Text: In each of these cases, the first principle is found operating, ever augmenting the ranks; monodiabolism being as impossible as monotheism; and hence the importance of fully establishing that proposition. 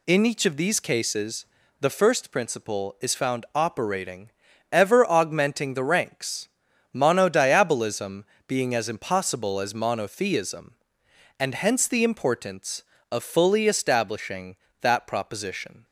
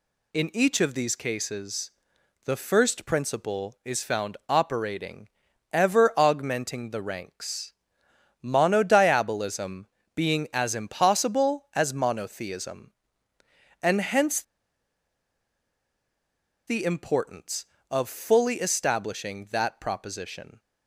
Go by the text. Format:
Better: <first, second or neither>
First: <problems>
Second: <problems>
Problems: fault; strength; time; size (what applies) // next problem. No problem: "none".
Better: first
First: pauses between "monodiabolism" and "being"; slight; at 8.2 s; 0.24 s long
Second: pauses between "monodiabolism" and "being"; slight; at 9.8 s; 0.30 s long // pauses between "hence" and "the"; strong; at 14.3 s; 2.2 s long